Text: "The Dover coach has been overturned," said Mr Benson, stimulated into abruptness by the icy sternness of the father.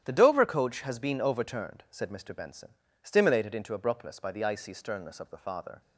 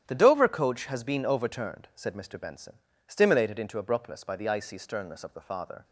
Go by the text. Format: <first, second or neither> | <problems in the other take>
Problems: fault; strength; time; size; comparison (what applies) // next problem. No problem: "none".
neither | starts louder than the rest; strong; the same in both